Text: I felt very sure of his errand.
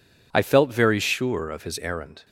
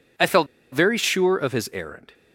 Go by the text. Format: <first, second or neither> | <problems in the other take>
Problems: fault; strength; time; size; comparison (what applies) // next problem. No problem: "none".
first | pauses between "felt" and "very"; slight; at 0.4 s; 0.26 s long